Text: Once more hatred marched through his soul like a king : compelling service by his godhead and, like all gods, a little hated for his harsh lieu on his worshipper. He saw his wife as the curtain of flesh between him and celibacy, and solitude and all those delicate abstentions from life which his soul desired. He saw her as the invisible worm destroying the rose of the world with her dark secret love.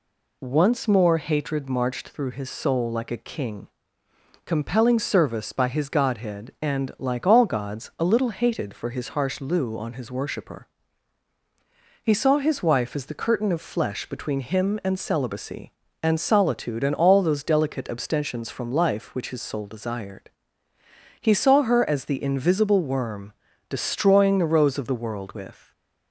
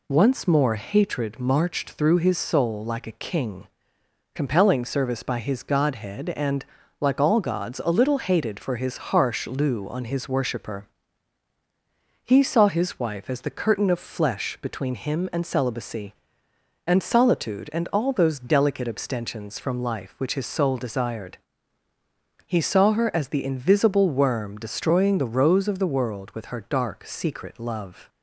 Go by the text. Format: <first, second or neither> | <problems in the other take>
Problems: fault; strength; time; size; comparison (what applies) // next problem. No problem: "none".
second | pauses between "worm" and "destroying"; at 23.3 s; 0.38 s long // stops before "her dark secret love"; at 25.7 s